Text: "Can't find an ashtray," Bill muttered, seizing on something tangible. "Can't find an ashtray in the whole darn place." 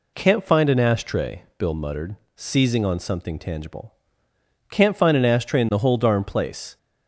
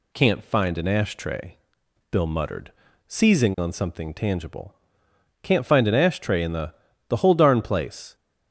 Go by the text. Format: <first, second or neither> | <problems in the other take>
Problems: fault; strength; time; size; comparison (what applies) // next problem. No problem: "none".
first | says "the" twice; at 7.0 s